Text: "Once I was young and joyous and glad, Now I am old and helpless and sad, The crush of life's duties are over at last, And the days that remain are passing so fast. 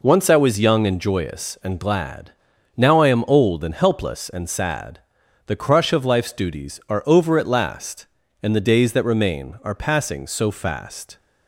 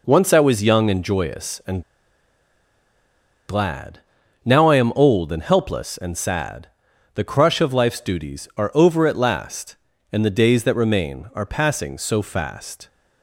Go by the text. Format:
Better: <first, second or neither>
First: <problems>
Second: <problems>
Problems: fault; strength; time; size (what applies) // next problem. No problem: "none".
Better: first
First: none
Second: pauses between "and" and "glad"; strong; at 1.8 s; 1.6 s long